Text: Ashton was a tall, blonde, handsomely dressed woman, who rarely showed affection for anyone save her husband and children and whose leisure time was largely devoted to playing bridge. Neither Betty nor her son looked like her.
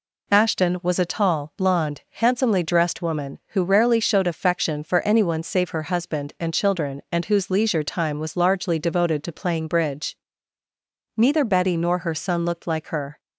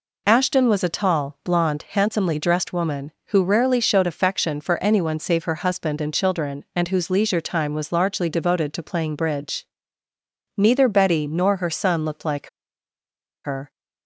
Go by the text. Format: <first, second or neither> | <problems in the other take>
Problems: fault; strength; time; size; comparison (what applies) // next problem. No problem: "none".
first | pauses between "like" and "her"; noticeable; at 12.4 s; 0.97 s long